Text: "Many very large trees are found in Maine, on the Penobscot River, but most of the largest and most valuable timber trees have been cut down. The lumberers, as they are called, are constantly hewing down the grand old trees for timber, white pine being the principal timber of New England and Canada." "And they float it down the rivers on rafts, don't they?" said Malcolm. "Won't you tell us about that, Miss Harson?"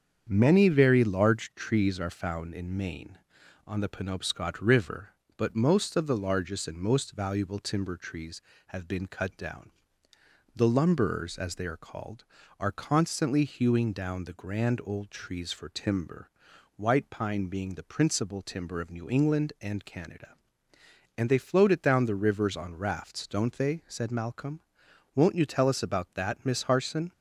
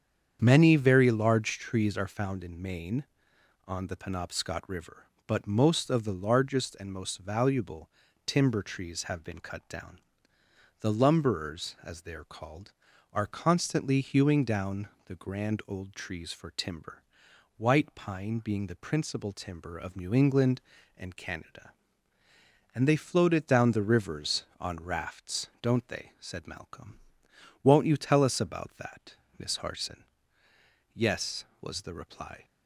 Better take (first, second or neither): first